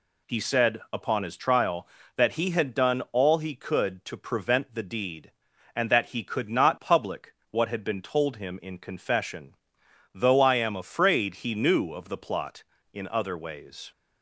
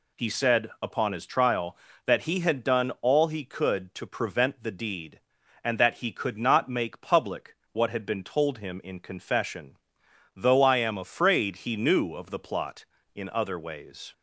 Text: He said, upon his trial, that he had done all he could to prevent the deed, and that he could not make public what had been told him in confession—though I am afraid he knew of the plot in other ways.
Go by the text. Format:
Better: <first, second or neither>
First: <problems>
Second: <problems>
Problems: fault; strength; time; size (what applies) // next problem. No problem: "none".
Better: second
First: skips "make"; at 6.7 s // pauses between "public" and "what"; slight; at 7.3 s; 0.18 s long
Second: pauses between "public" and "what"; slight; at 7.5 s; 0.18 s long